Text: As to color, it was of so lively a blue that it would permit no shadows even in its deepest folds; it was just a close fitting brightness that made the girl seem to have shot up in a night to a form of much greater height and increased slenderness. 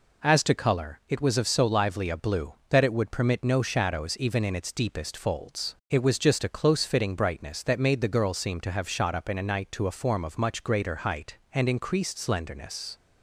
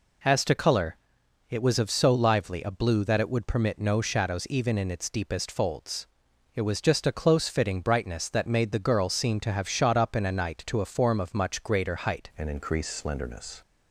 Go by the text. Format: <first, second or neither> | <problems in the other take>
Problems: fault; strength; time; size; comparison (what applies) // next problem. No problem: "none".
first | changes voice at "and"; from 12.3 s on; 1.3 s long